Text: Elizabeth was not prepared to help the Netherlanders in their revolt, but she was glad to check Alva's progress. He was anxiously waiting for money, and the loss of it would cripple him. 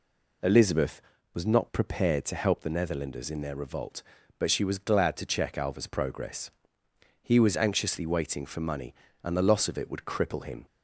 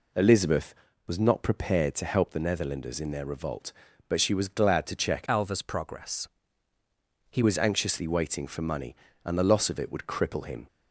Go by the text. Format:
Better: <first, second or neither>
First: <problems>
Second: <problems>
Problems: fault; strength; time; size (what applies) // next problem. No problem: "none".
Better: first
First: none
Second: changes voice from "Alva's" to "He"; from 5.2 to 7.4 s; 2.2 s long